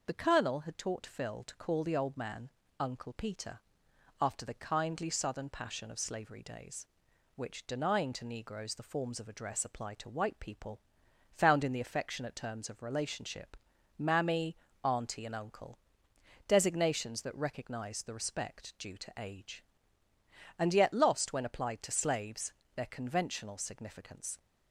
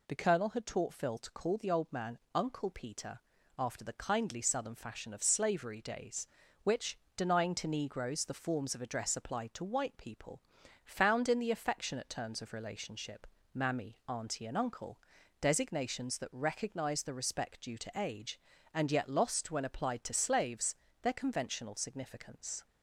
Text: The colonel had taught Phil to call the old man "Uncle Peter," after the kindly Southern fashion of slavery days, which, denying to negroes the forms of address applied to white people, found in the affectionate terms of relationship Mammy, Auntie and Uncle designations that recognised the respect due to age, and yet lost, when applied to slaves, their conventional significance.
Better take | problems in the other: second | pauses between "man" and "Uncle"; slight; at 2.4 s; 0.30 s long; slight in the second // says "passion" for "fashion"; at 5.4 s // pauses between "relationship" and "Mammy"; at 13.5 s; 0.42 s long; slight in the second // pauses between "Uncle" and "designations"; noticeable; at 15.7 s; 0.70 s long; also in the second

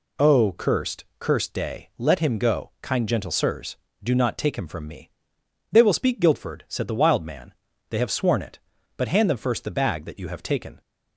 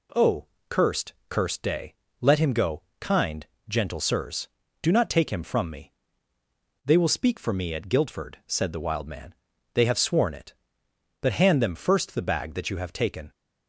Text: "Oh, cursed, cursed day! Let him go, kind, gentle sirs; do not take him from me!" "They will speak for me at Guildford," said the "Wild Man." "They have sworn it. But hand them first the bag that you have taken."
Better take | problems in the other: second | skips "for me at"; at 6.2 s

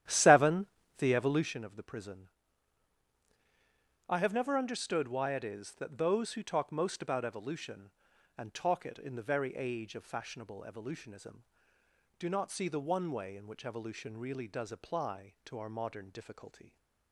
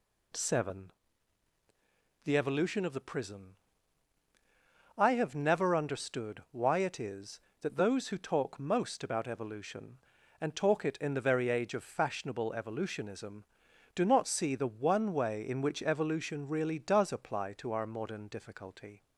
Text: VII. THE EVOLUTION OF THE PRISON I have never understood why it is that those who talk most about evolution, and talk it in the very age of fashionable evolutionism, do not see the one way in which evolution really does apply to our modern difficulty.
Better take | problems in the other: second | starts louder than the rest; strong; until 1.7 s; 11.5 dB // pauses between "PRISON" and "I"; strong; at 2.2 s; 1.8 s long; strong in the second

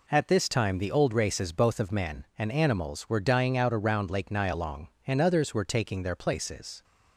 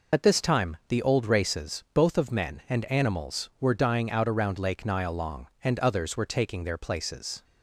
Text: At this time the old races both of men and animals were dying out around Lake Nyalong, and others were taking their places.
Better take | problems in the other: first | loses the start of "At"; at 0.1 s; 55 ms

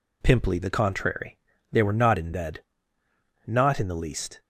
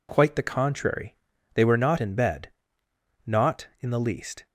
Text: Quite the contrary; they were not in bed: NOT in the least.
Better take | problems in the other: second | says "Pimply" for "Quite"; at 0.2 s

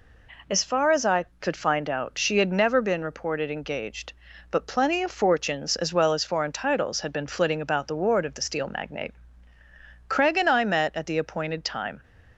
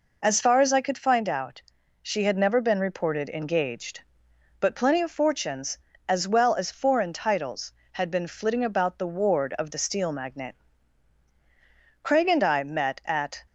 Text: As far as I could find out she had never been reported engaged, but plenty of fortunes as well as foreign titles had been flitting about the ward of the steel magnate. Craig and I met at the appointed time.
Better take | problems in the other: first | pauses between "out" and "she"; at 1.6 s; 0.40 s long // stops before "the appointed time"; at 13.4 s

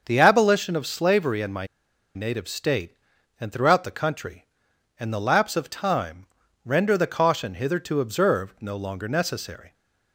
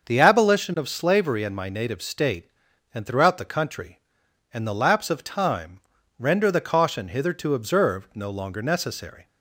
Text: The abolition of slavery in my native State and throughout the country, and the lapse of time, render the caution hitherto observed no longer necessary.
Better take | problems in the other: second | starts louder than the rest; until 1.0 s; 6 dB; also in the second // pauses between "my" and "native"; noticeable; at 1.6 s; 0.48 s long

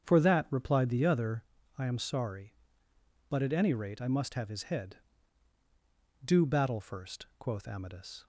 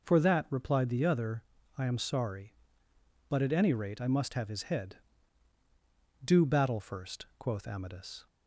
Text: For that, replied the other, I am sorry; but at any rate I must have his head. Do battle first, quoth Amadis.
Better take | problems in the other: second | starts louder than the rest; strong; until 1.5 s; 8 dB

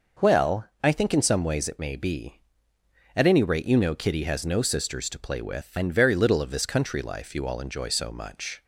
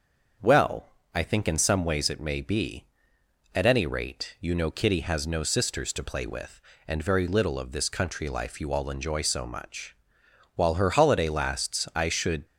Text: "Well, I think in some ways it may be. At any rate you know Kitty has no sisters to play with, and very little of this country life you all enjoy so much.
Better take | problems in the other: first | starts louder than the rest; until 1.6 s; 6.5 dB // goes on to say "While her holiday lasts I should"; strong; from 10.5 s on; 1.9 s long

